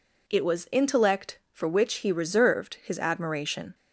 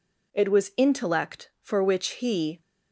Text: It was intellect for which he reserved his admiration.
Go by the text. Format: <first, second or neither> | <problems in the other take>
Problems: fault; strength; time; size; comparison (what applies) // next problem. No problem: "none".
first | stops before "reserved his admiration"; at 2.6 s